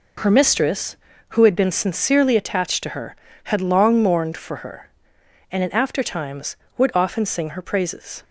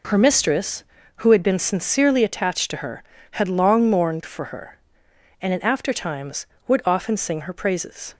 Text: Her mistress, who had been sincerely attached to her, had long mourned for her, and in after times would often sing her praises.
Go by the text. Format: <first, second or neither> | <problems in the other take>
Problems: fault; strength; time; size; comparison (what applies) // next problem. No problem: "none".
neither | none